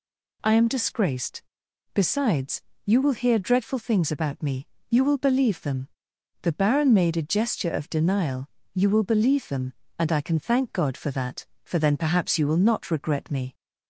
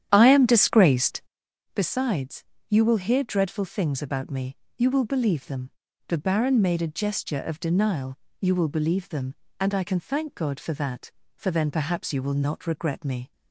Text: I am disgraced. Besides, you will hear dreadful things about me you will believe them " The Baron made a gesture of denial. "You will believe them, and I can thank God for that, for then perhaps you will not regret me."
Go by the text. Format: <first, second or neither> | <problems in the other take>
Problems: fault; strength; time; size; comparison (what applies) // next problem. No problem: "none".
first | starts louder than the rest; strong; until 1.4 s; 10.5 dB // pauses between "me" and "you"; slight; at 4.5 s; 0.24 s long; slight in the first